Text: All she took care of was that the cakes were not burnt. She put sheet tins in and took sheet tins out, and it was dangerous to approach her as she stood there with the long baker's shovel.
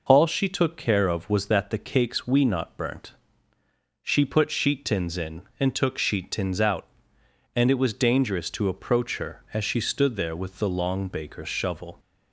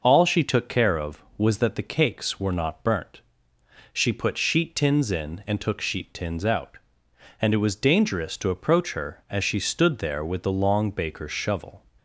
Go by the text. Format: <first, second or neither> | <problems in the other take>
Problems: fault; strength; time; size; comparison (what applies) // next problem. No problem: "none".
second | says "we" for "were"; at 2.2 s